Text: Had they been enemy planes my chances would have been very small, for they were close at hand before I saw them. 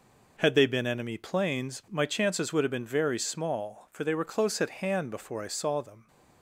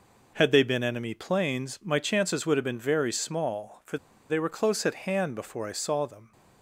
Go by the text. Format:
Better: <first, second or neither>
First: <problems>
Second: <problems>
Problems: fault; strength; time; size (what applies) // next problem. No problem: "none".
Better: first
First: none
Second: pauses between "for" and "they"; slight; at 3.9 s; 0.33 s long